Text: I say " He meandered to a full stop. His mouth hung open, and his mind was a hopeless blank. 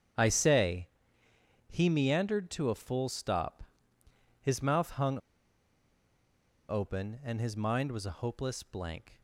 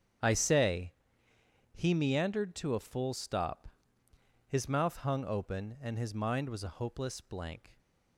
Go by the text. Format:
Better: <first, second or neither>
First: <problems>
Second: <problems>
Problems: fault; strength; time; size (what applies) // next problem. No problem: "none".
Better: second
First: starts louder than the rest; until 1.5 s; 7 dB // pauses between "hung" and "open"; strong; at 5.1 s; 1.5 s long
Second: starts louder than the rest; until 1.6 s; 7 dB